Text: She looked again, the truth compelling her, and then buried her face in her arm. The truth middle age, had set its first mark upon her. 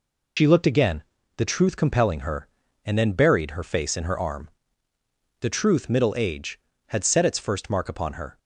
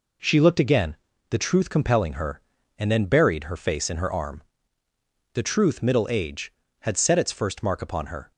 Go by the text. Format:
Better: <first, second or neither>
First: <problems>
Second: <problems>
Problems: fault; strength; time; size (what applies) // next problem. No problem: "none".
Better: second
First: loses the start of "She"; at 0.3 s; 80 ms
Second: none